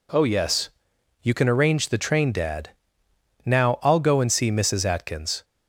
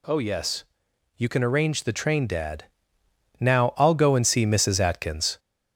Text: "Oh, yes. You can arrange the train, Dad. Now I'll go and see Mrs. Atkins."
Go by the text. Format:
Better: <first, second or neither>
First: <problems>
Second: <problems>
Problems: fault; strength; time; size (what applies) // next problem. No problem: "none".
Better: first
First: none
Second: gets louder; slight; throughout; 2 dB